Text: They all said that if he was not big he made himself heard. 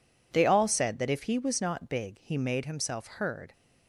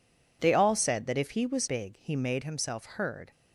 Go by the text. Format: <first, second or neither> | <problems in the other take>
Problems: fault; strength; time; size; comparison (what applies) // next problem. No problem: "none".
first | skips "not"; at 1.6 s